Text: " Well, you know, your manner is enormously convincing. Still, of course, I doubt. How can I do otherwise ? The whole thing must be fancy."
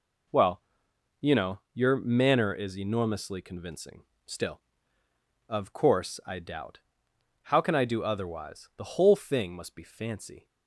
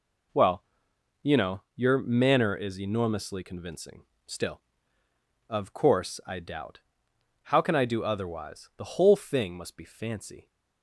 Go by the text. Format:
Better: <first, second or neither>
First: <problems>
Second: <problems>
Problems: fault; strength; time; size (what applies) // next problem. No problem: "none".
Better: neither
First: none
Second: none